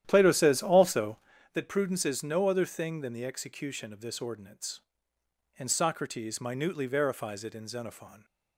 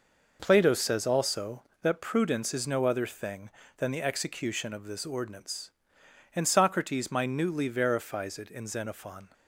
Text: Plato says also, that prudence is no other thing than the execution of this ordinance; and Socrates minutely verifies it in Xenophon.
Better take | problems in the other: second | starts louder than the rest; strong; until 1.5 s; 11 dB

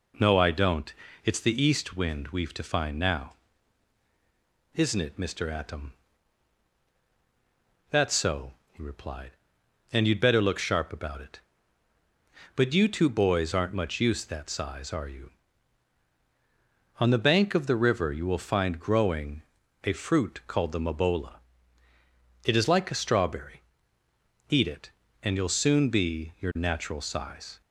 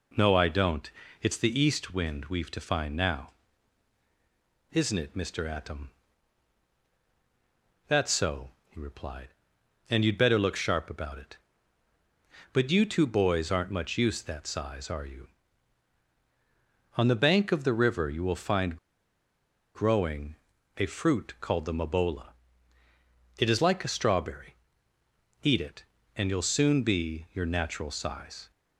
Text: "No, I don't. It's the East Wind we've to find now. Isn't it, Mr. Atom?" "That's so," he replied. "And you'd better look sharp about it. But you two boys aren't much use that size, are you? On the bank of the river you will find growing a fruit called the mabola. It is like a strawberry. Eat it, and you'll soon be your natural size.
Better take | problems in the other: first | pauses between "find" and "growing"; at 18.7 s; 0.98 s long // pauses between "growing" and "a"; at 20.3 s; 0.40 s long; also in the first

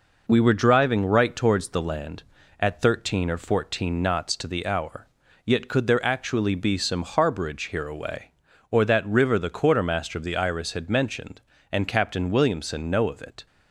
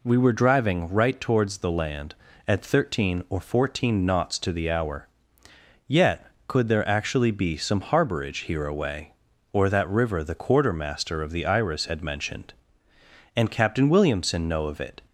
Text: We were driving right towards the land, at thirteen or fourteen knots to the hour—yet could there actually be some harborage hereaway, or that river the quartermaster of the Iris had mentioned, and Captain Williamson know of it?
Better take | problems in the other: neither | none

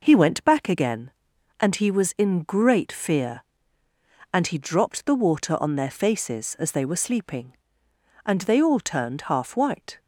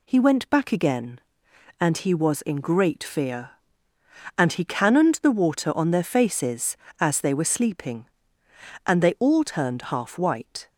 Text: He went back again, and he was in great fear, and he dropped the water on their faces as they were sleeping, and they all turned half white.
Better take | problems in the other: first | says "cannoned" for "dropped"; at 4.6 s

